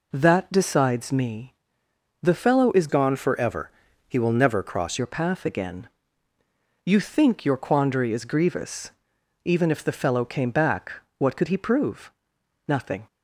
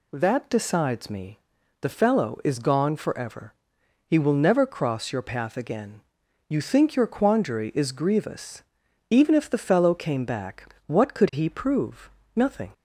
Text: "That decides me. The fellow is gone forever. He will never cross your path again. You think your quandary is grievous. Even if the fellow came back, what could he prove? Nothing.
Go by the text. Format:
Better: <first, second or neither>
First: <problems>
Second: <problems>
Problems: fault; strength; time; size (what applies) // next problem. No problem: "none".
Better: second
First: changes voice from "gone" to "cross"; from 2.8 to 4.9 s; 2.1 s long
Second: none